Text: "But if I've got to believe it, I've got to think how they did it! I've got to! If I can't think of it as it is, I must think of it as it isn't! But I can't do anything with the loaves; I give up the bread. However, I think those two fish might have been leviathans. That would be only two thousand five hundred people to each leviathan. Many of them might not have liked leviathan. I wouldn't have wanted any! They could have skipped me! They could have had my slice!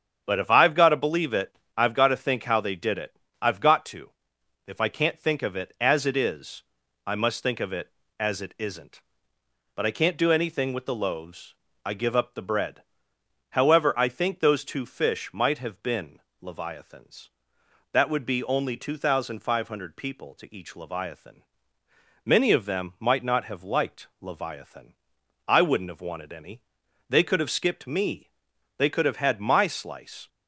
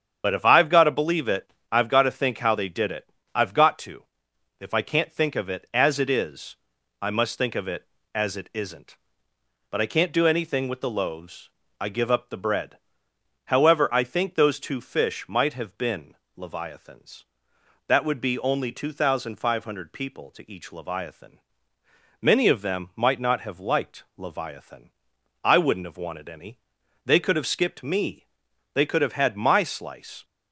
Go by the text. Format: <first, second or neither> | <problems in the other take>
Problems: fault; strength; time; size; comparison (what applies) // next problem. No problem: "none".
first | loses the start of "But"; at 0.2 s; 50 ms // starts louder than the rest; strong; until 1.2 s; 8 dB; strong in the first // pauses between "been" and "leviathans"; slight; at 16.1 s; 0.22 s long; slight in the first